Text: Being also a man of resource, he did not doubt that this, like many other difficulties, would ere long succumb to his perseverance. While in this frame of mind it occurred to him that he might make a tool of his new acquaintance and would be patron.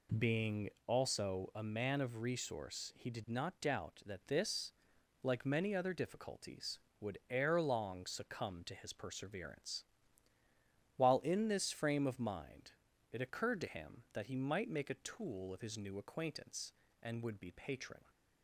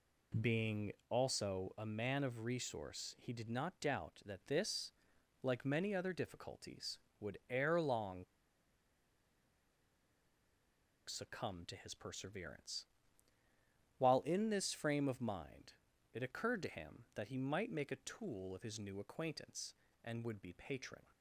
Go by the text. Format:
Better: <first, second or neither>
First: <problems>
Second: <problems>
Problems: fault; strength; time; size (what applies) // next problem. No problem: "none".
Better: first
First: pauses between "Being" and "also"; slight; at 0.7 s; 0.16 s long // pauses between "mind" and "it"; at 12.7 s; 0.40 s long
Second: pauses between "Being" and "also"; slight; at 0.9 s; 0.16 s long // pauses between "long" and "succumb"; strong; at 8.2 s; 2.8 s long // pauses between "mind" and "it"; at 15.7 s; 0.40 s long